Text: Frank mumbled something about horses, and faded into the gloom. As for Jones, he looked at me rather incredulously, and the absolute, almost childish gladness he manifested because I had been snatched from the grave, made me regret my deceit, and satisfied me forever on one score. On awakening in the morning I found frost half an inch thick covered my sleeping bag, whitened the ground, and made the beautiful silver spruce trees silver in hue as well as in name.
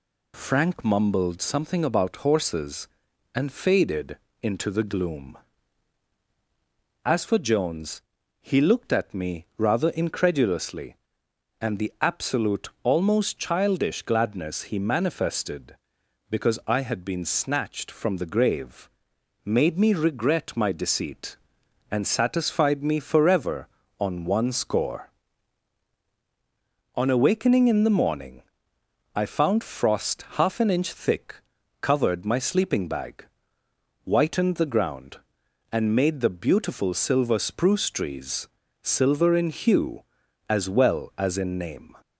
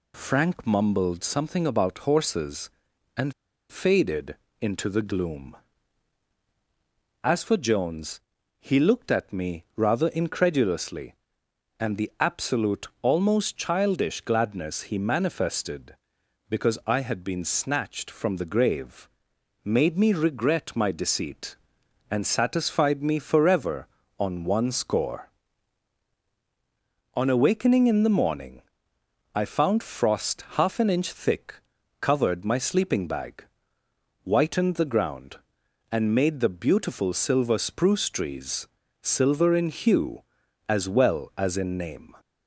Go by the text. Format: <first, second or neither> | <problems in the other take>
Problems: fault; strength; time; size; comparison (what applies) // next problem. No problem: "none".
first | pauses between "and" and "faded"; at 3.3 s; 0.40 s long // pauses between "faded" and "into"; slight; at 4.3 s; 0.24 s long; slight in the first // pauses between "morning" and "I"; noticeable; at 28.5 s; 0.74 s long; noticeable in the first // pauses between "thick" and "covered"; noticeable; at 31.5 s; 0.48 s long; noticeable in the first // pauses between "trees" and "silver"; slight; at 38.6 s; 0.32 s long; slight in the first